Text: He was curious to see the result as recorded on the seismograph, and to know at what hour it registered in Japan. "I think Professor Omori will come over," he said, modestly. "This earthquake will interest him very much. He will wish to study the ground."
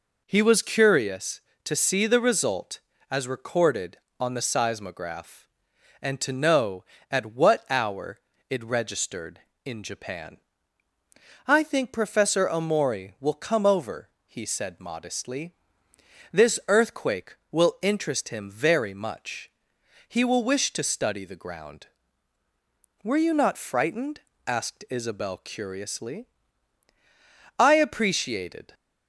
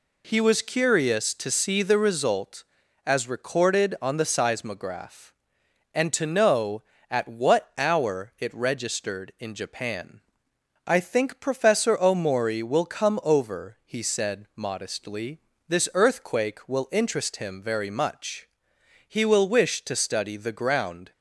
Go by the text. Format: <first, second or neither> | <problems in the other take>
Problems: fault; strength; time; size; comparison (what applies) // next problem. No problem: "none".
second | pauses between "hour" and "it"; slight; at 8.1 s; 0.30 s long // goes on to say "Were you not frightened asked Isabel curiously I appreciated"; strong; from 23.0 s on; 5.7 s long